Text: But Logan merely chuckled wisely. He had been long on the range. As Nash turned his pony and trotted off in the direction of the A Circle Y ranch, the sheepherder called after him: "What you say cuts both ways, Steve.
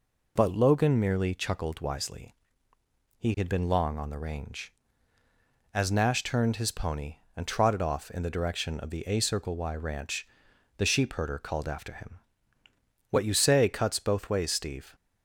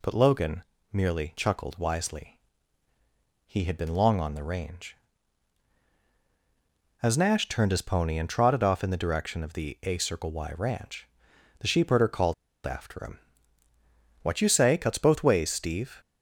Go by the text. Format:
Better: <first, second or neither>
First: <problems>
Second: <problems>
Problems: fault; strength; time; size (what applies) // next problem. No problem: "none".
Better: first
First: none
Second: pauses between "Logan" and "merely"; slight; at 0.6 s; 0.30 s long // pauses between "called" and "after"; slight; at 12.3 s; 0.31 s long